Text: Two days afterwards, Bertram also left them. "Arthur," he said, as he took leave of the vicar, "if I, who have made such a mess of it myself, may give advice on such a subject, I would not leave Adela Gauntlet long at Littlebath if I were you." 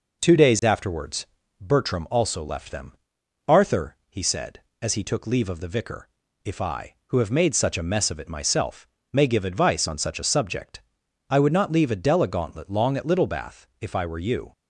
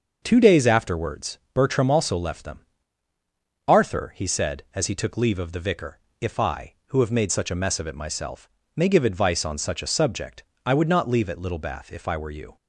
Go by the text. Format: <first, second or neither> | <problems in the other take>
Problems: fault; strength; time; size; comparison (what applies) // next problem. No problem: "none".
first | starts louder than the rest; until 1.2 s; 6 dB // skips "Adela Gauntlet long"; at 11.2 s